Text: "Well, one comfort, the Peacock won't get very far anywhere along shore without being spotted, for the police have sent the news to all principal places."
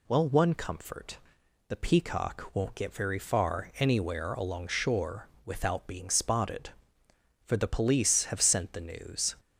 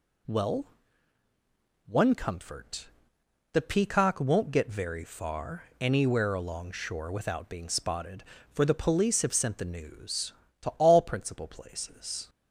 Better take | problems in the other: second | pauses between "shore" and "without"; slight; at 5.2 s; 0.18 s long // stops before "to all principal places"; at 9.3 s

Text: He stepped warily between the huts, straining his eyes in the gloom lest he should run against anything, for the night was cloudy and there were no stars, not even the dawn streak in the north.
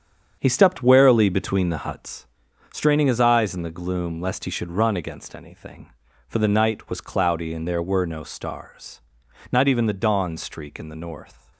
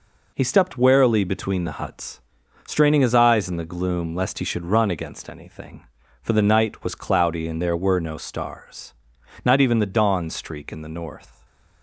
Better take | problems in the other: second | starts louder than the rest; strong; until 2.0 s; 7.5 dB

